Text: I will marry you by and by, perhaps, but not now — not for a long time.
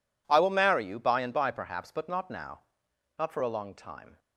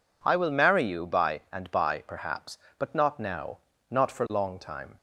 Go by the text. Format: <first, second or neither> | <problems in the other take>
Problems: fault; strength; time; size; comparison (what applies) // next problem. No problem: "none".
first | skips "a"; at 4.2 s